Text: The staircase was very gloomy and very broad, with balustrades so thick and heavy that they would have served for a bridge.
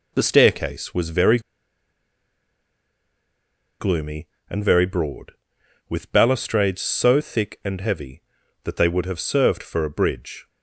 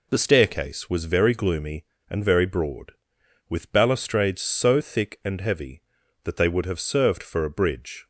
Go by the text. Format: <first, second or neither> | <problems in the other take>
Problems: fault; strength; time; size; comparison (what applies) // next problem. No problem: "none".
second | pauses between "very" and "gloomy"; strong; at 1.3 s; 2.4 s long